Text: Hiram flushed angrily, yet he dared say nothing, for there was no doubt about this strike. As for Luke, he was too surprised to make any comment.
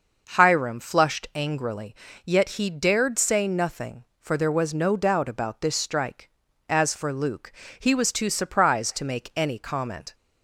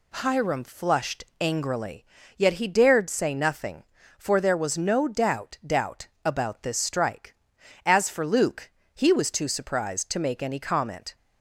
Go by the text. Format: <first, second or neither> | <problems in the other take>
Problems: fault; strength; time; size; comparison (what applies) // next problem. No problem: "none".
first | pauses between "flushed" and "angrily"; slight; at 1.2 s; 0.16 s long // says "doubt" twice; at 5.6 s